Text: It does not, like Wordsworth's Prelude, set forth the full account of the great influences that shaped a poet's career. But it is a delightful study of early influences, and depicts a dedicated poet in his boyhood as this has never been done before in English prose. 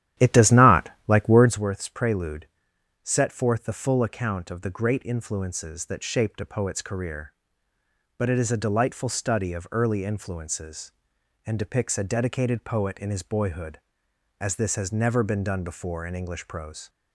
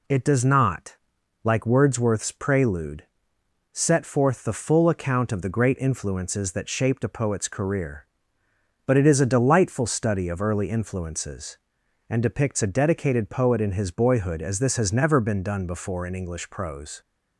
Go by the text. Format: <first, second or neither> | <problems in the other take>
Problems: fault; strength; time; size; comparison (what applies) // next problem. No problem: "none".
second | starts louder than the rest; strong; until 1.7 s; 12 dB